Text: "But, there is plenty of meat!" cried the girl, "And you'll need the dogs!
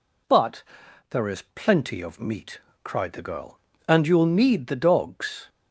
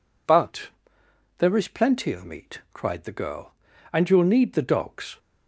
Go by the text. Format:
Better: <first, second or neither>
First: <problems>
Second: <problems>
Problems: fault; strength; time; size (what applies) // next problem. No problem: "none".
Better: neither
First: none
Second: none